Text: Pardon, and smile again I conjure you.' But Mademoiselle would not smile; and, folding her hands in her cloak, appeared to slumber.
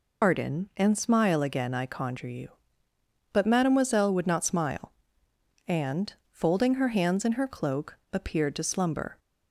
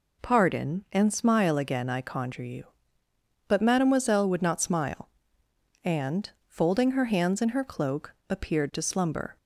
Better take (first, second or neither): second